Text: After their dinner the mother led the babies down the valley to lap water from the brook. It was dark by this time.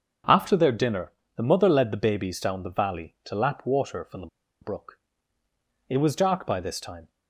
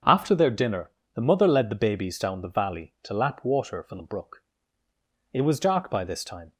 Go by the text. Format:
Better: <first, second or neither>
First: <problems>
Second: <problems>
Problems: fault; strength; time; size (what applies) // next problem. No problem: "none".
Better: second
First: starts louder than the rest; until 1.5 s; 6.5 dB // pauses between "dinner" and "the"; slight; at 1.1 s; 0.24 s long // pauses between "the" and "brook"; slight; at 4.2 s; 0.34 s long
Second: starts louder than the rest; until 1.3 s; 6.5 dB // pauses between "dinner" and "the"; slight; at 0.8 s; 0.24 s long